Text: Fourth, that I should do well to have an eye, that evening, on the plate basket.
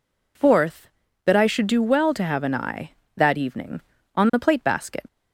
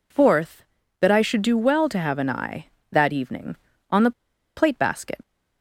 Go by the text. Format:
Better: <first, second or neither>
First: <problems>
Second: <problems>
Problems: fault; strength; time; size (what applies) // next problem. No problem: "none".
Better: first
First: none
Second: pauses between "the" and "plate"; at 4.1 s; 0.45 s long